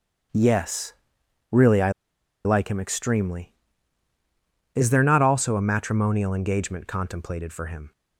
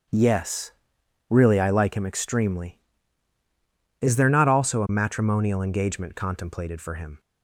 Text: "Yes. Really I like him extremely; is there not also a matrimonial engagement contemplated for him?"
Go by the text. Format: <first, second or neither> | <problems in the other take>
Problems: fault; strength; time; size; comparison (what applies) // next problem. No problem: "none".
second | starts louder than the rest; strong; until 1.8 s; 7.5 dB; strong in the second // pauses between "I" and "like"; noticeable; at 1.8 s; 0.55 s long